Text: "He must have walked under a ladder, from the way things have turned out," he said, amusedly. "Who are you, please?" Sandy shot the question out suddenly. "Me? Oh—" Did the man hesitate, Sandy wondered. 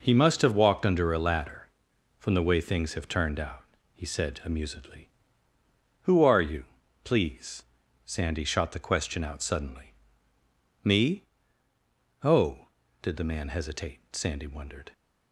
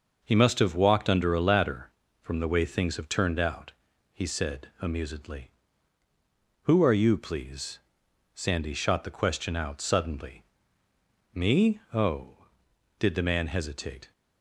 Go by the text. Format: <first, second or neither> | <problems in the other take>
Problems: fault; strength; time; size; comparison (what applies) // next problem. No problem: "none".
first | stops before "Sandy wondered"; at 14.1 s